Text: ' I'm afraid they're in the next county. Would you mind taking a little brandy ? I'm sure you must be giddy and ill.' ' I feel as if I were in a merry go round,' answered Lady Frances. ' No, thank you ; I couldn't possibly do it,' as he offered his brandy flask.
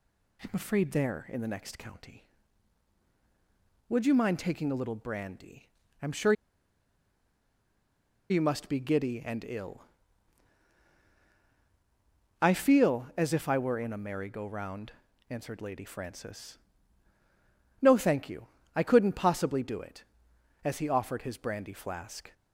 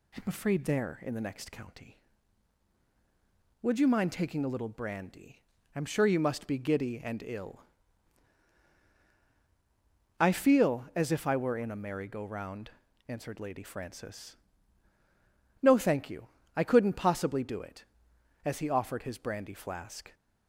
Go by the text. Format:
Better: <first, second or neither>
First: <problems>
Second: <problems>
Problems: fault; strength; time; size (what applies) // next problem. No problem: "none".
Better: second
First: pauses between "sure" and "you"; strong; at 6.3 s; 1.9 s long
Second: none